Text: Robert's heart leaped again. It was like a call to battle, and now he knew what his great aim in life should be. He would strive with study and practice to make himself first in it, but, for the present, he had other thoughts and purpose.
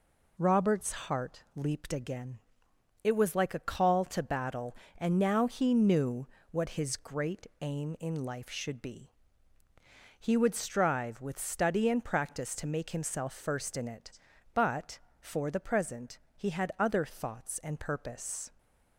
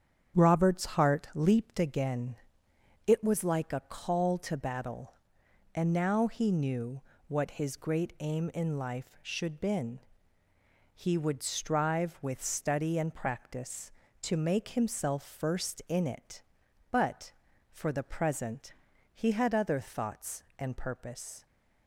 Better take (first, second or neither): first